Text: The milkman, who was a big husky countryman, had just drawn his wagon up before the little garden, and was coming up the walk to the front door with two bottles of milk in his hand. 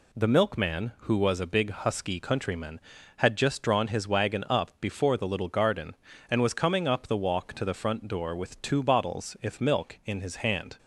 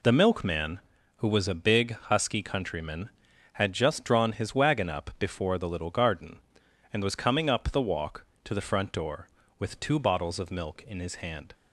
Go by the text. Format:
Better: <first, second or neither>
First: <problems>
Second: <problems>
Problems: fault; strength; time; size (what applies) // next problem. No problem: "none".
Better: second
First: says "if" for "of"; at 9.4 s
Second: none